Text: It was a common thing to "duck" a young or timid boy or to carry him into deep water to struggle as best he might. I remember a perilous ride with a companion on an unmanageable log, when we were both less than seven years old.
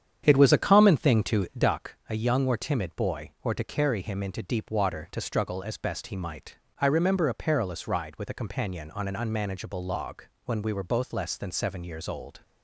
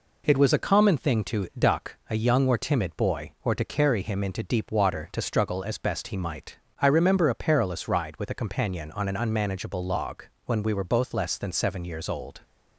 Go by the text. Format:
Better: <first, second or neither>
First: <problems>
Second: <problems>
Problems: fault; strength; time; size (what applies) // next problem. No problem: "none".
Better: second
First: starts louder than the rest; strong; until 1.7 s; 8.5 dB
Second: none